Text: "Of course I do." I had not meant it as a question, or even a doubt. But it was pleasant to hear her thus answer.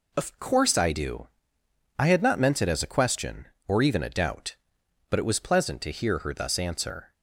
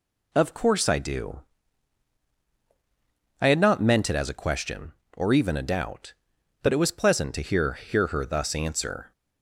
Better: first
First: none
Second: says "hear" twice; at 7.7 s

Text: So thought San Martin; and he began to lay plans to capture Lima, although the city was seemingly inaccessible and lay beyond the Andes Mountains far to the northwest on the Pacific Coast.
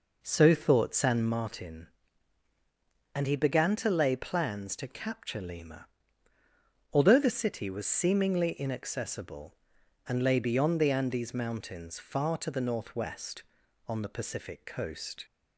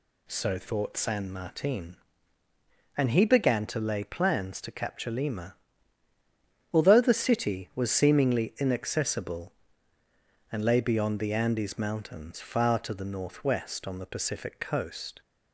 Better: second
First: starts louder than the rest; noticeable; until 1.4 s; 4.5 dB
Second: none

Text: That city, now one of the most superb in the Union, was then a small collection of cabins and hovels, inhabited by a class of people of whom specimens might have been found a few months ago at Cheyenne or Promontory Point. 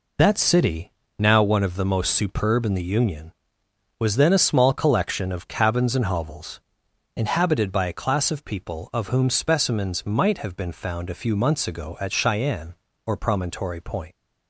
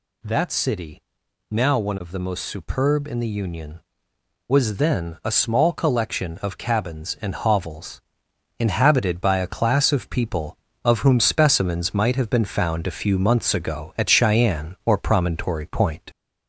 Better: first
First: none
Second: gets louder; slight; throughout; 2.5 dB

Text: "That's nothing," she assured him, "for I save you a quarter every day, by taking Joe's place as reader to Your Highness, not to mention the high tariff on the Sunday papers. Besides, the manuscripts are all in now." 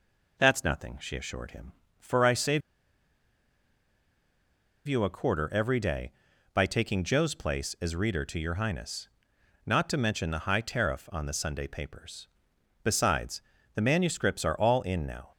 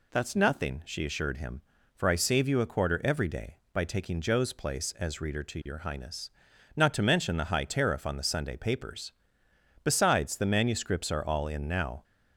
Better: second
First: pauses between "save" and "you"; strong; at 2.6 s; 2.2 s long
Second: none

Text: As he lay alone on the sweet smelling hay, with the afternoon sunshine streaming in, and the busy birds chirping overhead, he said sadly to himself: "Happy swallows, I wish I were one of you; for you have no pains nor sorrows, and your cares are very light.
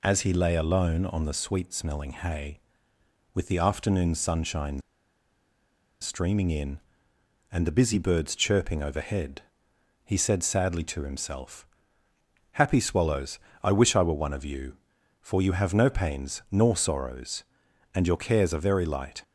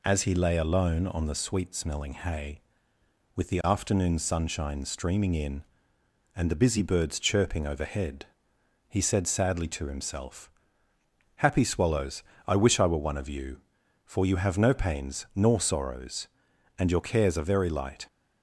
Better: second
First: pauses between "sunshine" and "streaming"; at 4.8 s; 1.2 s long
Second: none

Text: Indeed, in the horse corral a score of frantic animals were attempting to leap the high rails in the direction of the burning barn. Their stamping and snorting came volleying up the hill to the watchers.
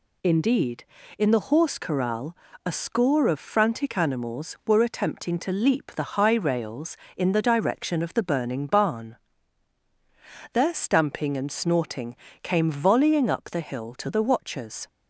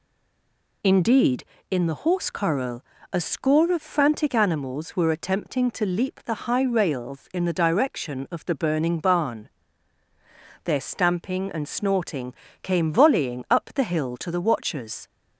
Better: first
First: pauses between "corral" and "a"; slight; at 2.3 s; 0.30 s long // pauses between "snorting" and "came"; slight; at 12.1 s; 0.26 s long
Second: stays silent before the first word; slight; until 0.8 s; 0.8 s long // pauses between "corral" and "a"; slight; at 2.8 s; 0.28 s long // pauses between "snorting" and "came"; slight; at 12.3 s; 0.28 s long

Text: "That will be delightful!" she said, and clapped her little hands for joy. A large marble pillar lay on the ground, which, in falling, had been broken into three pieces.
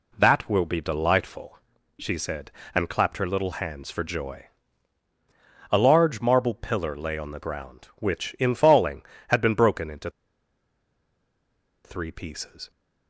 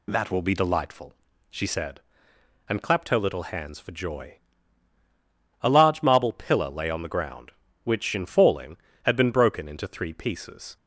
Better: second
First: pauses between "into" and "three"; strong; at 10.1 s; 1.7 s long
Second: none

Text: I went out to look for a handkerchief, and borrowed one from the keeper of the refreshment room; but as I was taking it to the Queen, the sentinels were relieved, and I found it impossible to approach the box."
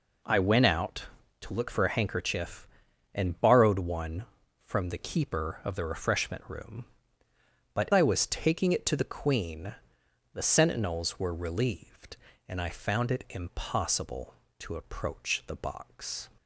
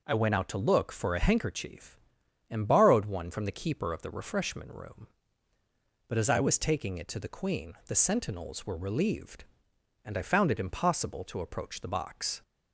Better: second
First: skips "as"; at 7.9 s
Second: none

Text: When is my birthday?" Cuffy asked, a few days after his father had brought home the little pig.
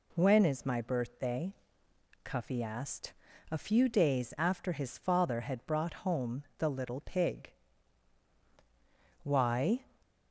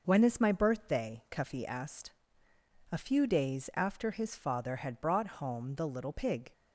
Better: second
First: pauses between "home" and "the"; slight; at 6.4 s; 0.16 s long // goes on to say "Why"; noticeable; from 9.2 s on; 0.62 s long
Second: none

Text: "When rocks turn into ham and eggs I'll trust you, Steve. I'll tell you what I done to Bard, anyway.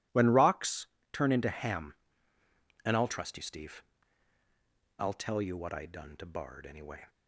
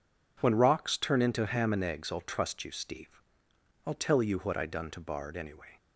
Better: second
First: pauses between "rocks" and "turn"; slight; at 0.8 s; 0.26 s long // skips "eggs"; at 2.9 s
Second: none

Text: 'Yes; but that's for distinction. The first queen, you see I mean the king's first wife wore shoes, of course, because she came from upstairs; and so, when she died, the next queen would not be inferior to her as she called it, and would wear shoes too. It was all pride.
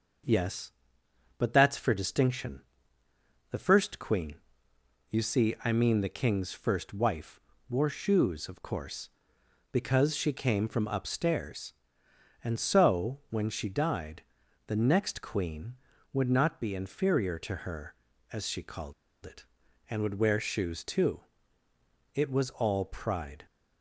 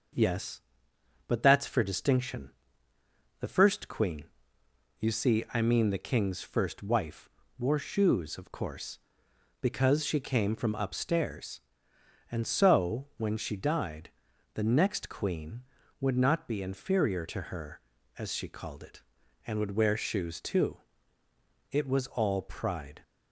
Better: second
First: pauses between "wife" and "wore"; slight; at 7.4 s; 0.28 s long // pauses between "called" and "it"; slight; at 18.9 s; 0.31 s long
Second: pauses between "wife" and "wore"; slight; at 7.2 s; 0.28 s long

